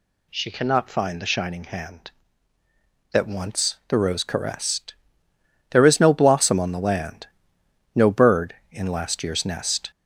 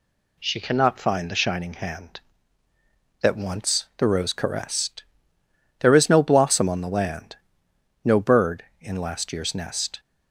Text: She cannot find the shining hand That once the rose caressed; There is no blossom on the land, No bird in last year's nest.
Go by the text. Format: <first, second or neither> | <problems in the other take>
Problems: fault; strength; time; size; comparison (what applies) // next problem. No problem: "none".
second | gets louder; slight; throughout; 3 dB